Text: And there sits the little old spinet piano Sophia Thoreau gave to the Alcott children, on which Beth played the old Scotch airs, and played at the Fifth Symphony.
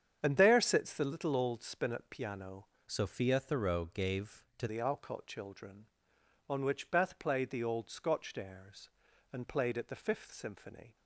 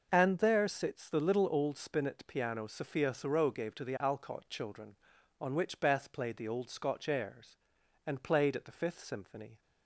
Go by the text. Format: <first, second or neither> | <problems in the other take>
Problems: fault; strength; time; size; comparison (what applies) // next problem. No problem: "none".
second | starts louder than the rest; strong; until 1.2 s; 8 dB // changes voice from "Sophia" to "to"; from 2.8 to 4.6 s; 1.8 s long